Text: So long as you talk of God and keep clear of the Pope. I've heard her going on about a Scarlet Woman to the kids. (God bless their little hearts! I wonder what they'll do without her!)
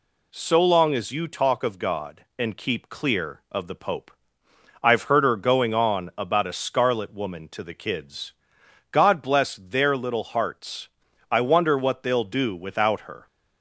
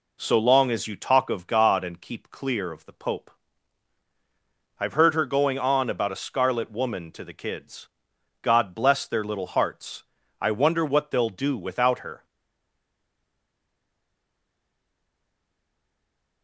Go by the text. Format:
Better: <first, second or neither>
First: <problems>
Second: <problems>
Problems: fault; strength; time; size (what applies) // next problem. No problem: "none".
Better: first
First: none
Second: stays silent after the last word; strong; from 12.2 s on; 4.2 s long